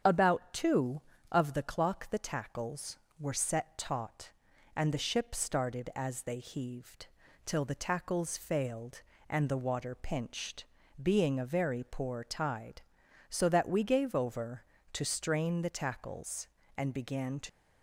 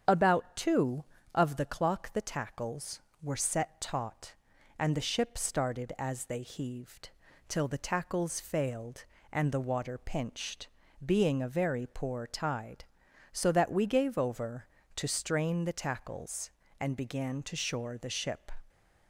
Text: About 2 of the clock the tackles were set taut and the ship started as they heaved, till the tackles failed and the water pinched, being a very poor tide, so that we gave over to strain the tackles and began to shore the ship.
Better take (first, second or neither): second